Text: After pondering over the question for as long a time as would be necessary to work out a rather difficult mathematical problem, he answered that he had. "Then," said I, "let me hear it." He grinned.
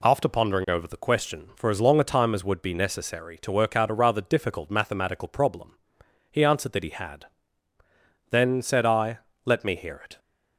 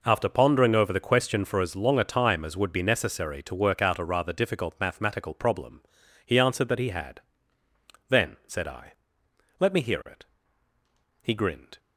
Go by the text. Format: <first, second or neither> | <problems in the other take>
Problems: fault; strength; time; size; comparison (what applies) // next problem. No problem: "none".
second | stops before "He grinned"; at 10.1 s